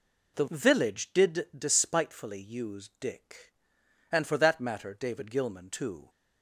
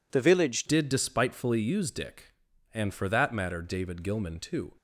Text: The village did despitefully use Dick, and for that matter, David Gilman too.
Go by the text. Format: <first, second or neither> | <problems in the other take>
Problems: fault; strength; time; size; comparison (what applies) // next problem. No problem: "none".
first | changes voice at "did"; from 0.6 s on; 4.1 s long